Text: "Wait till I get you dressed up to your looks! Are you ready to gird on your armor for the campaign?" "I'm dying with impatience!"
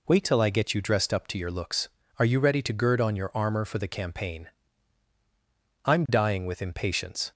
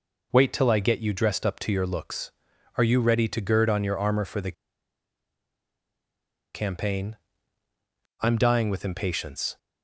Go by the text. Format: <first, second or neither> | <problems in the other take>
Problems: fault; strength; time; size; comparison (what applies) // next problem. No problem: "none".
first | pauses between "the" and "campaign"; strong; at 4.5 s; 2.0 s long